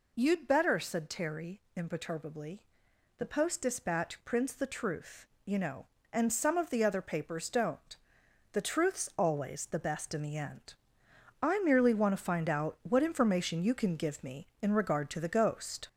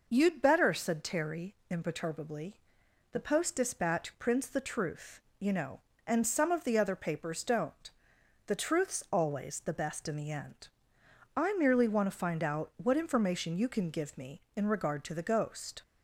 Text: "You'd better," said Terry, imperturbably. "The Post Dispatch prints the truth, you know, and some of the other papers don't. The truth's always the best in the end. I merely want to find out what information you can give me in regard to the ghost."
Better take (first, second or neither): second